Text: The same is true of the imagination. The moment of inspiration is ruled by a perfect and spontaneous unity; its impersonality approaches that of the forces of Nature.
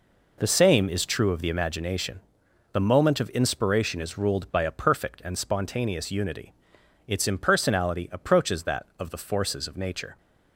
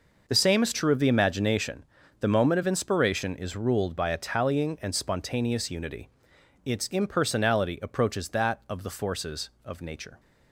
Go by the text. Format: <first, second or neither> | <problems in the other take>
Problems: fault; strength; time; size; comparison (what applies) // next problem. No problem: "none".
first | says "tallying" for "perfect"; at 4.1 s